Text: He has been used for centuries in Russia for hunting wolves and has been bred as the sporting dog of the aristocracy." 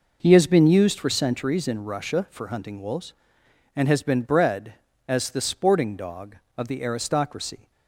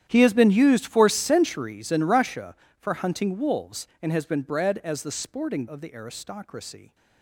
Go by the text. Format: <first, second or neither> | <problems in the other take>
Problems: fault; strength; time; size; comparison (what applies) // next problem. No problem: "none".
first | starts louder than the rest; strong; until 1.0 s; 10.5 dB // skips "dog"; at 5.6 s